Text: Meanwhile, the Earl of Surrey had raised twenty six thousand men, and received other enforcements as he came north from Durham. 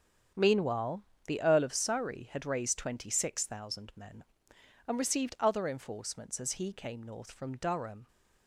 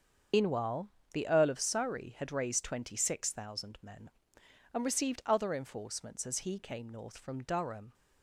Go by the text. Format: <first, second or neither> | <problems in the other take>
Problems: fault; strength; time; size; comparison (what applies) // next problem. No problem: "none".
first | loses the start of "Meanwhile"; at 0.3 s; 125 ms // starts louder than the rest; until 1.5 s; 7 dB; strong in the first